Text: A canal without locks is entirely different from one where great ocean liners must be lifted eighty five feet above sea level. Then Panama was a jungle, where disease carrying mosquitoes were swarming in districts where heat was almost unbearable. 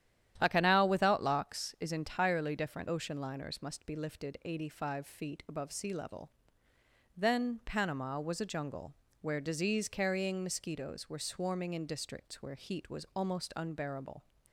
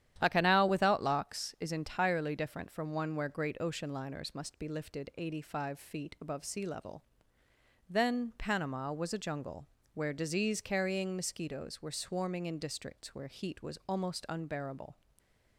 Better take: second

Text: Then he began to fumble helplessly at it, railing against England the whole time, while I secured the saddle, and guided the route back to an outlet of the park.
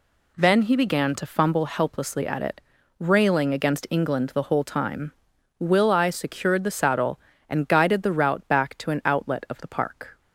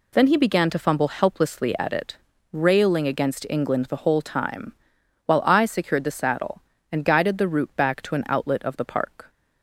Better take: second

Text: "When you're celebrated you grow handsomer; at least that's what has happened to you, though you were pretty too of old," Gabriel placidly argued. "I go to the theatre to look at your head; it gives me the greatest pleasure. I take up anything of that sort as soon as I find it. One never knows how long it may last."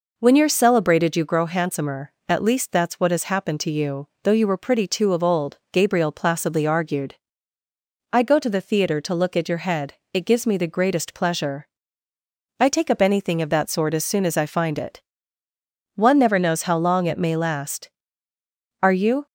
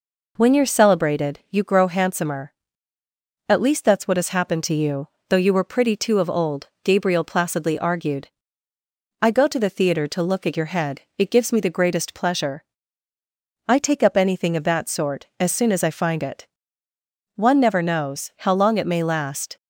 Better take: second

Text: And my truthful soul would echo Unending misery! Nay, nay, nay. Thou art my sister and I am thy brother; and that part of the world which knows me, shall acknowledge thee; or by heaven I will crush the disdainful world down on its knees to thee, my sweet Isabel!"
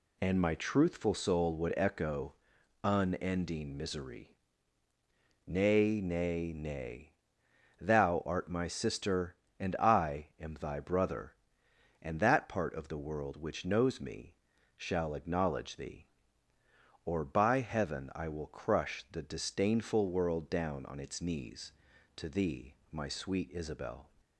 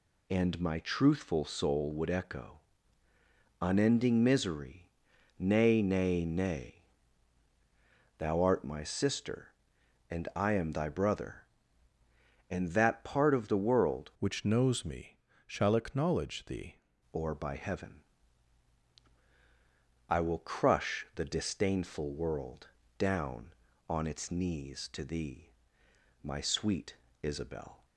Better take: first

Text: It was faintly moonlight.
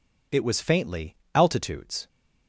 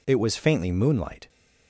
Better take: second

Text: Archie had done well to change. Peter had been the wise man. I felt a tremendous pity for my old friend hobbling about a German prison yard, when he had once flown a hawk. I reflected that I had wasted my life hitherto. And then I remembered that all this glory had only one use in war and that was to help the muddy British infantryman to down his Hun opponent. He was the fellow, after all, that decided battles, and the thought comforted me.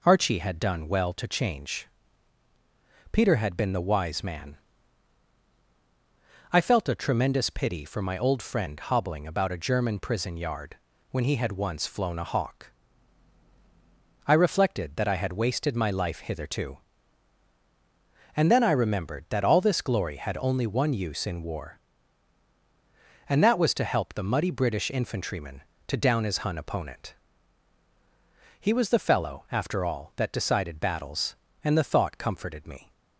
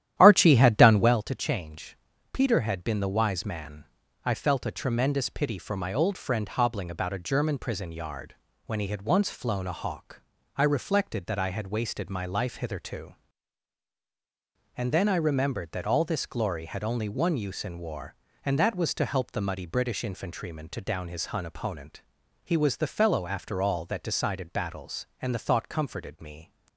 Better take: first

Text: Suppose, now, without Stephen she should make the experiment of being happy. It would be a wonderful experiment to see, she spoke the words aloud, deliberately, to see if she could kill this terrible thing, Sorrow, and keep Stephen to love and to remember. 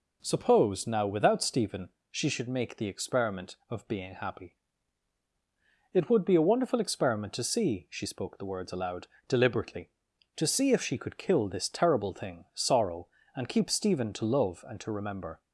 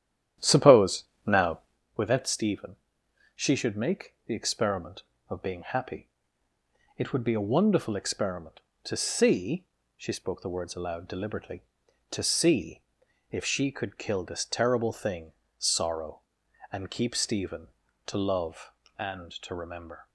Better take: first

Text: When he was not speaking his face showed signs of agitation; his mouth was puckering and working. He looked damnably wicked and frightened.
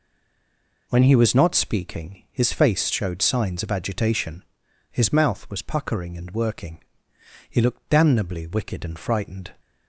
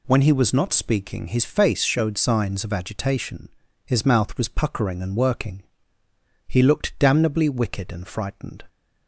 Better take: second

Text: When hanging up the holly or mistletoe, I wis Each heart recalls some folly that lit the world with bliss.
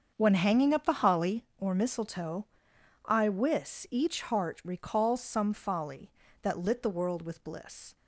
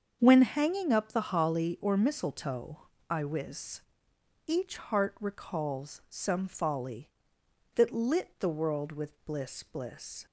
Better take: first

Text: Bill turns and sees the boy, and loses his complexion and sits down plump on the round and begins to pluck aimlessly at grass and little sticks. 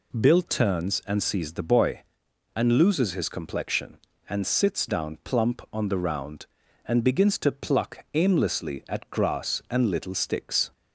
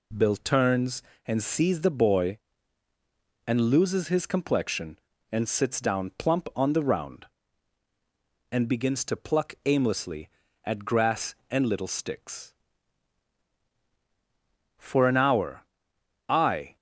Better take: first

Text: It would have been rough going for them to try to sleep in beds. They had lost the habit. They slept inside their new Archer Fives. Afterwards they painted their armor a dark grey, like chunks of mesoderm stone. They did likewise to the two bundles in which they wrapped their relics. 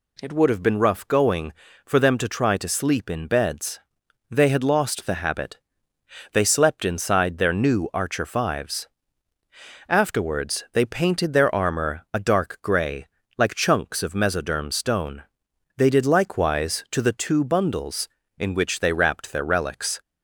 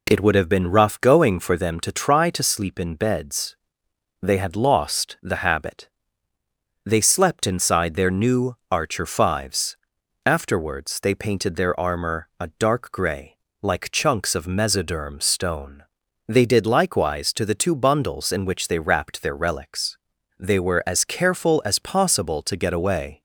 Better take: first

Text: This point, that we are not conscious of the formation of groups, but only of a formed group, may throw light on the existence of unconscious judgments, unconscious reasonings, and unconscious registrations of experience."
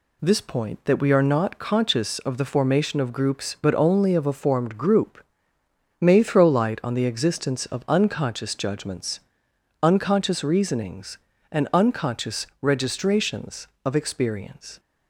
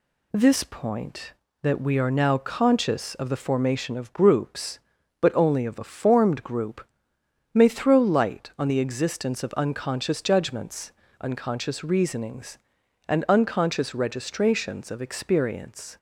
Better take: first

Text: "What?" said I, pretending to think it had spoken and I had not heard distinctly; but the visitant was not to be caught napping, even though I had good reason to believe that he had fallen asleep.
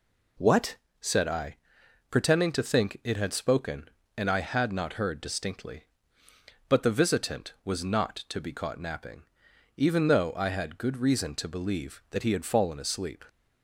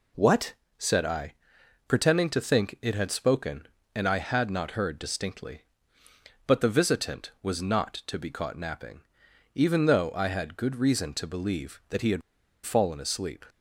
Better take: first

